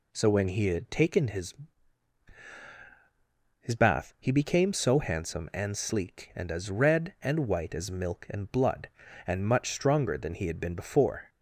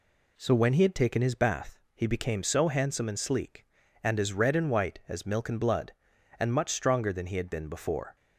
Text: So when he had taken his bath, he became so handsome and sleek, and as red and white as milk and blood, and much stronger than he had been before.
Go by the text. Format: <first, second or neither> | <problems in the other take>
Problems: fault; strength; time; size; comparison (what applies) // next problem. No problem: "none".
second | says "his" twice; at 3.6 s